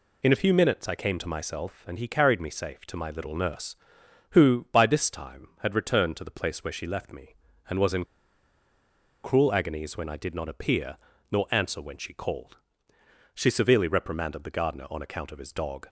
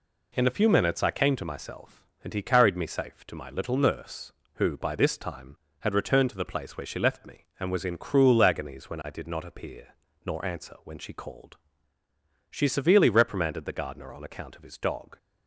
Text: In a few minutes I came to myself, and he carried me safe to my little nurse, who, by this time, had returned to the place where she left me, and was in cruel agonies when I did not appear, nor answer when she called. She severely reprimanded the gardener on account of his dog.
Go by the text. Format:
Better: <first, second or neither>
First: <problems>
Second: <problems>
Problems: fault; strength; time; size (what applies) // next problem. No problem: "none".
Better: second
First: pauses between "in" and "cruel"; at 8.0 s; 1.2 s long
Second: none